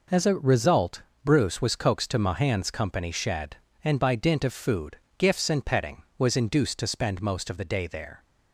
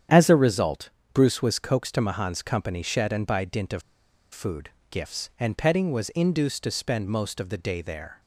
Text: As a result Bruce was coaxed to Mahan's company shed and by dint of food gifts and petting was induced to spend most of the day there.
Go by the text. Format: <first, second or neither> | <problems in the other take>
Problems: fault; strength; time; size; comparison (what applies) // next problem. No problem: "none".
first | starts louder than the rest; strong; until 1.3 s; 9 dB // pauses between "result" and "Bruce"; slight; at 0.9 s; 0.24 s long; slight in the first // pauses between "of" and "food"; noticeable; at 3.8 s; 0.51 s long // pauses between "food" and "gifts"; slight; at 4.6 s; 0.22 s long; slight in the first